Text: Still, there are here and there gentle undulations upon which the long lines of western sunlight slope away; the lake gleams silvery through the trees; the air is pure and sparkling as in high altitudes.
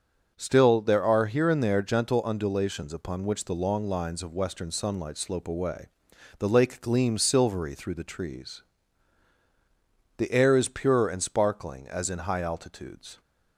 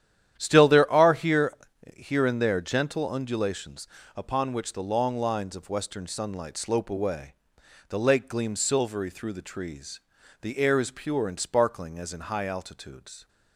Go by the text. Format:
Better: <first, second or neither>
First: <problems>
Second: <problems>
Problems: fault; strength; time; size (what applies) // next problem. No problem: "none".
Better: first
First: starts louder than the rest; noticeable; until 1.3 s; 6 dB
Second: starts louder than the rest; strong; until 1.3 s; 10.5 dB // says "here" twice; at 1.9 s // pauses between "undulations" and "upon"; slight; at 3.8 s; 0.30 s long